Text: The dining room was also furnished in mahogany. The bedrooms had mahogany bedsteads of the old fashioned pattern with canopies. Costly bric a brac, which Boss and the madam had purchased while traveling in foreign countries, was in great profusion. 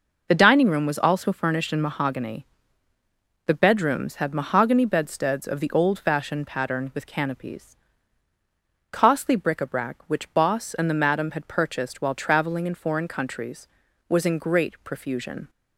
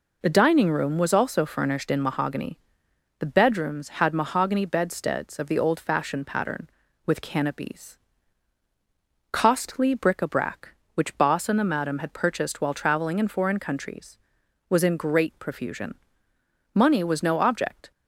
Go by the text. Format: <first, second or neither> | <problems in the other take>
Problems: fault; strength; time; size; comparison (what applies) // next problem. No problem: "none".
first | goes on to say "Money was no object"; noticeable; from 16.7 s on; 1.1 s long